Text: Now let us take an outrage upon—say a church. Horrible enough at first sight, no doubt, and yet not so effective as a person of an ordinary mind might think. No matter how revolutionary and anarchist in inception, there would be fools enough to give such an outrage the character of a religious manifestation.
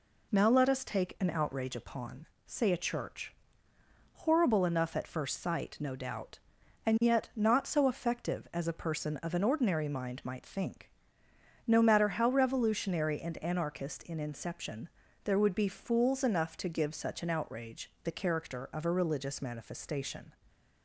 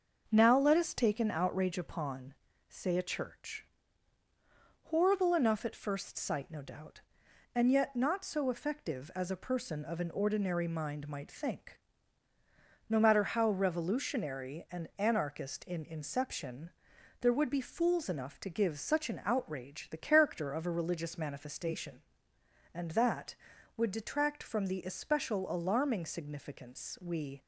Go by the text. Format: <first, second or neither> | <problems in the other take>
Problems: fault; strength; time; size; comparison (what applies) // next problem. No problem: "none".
first | starts louder than the rest; until 1.3 s; 6.5 dB // goes on to say "And that would detract from the especial alarming significance we"; strong; from 22.7 s on; 4.6 s long